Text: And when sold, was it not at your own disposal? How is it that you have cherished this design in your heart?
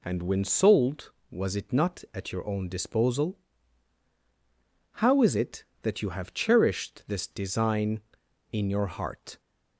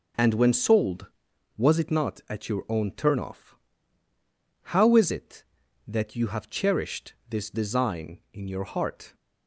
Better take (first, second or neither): first